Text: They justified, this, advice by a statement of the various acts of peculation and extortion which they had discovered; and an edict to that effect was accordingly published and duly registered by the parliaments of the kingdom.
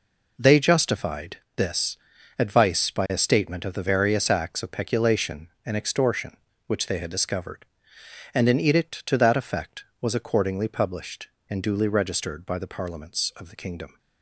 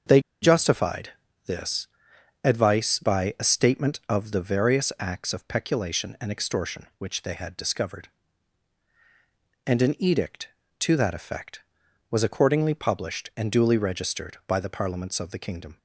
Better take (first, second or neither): first